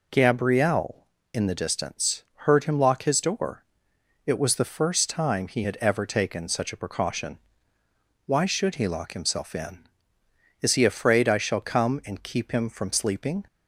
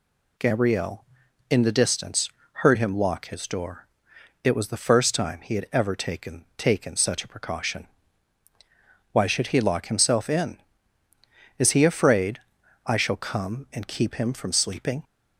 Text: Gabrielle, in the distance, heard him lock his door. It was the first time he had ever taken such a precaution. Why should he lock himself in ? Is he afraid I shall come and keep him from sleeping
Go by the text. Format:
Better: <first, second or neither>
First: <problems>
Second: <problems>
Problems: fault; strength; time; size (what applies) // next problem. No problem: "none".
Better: first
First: none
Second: says "taken" twice; at 6.5 s // pauses between "afraid" and "I"; noticeable; at 12.3 s; 0.46 s long